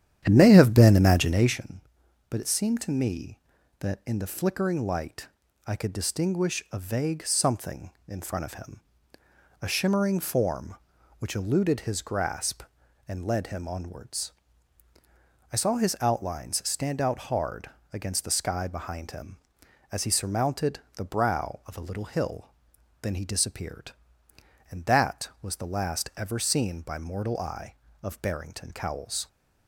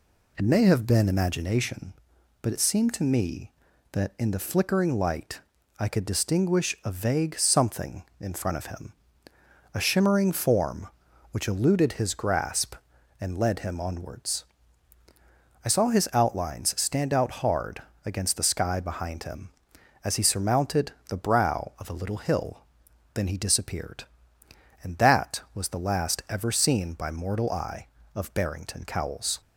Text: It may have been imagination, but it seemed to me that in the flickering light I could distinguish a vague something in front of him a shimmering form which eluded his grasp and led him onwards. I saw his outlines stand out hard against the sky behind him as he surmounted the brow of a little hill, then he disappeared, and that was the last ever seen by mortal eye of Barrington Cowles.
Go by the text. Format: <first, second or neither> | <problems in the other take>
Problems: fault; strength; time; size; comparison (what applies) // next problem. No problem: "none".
second | starts louder than the rest; strong; until 1.6 s; 10 dB // pauses between "light" and "I"; at 5.2 s; 0.40 s long; also in the second // pauses between "him" and "a"; noticeable; at 8.7 s; 0.82 s long; noticeable in the second // pauses between "hard" and "against"; slight; at 17.6 s; 0.24 s long; slight in the second // pauses between "surmounted" and "the"; slight; at 20.7 s; 0.16 s long; slight in the second